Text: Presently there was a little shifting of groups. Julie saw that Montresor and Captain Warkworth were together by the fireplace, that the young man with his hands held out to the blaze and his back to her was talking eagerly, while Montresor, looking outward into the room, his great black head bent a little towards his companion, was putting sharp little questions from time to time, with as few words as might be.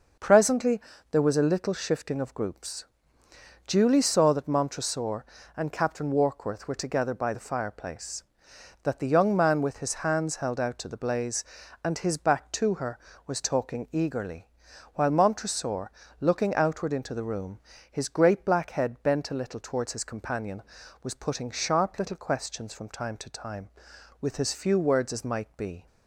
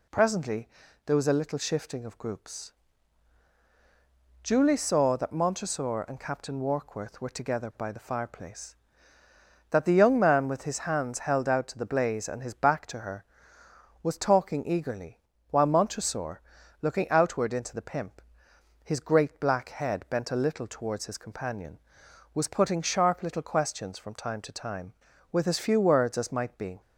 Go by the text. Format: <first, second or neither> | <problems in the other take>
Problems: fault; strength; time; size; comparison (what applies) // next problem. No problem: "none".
first | pauses between "Presently" and "there"; at 0.6 s; 0.38 s long; slight in the first // says "pimp" for "room"; at 17.8 s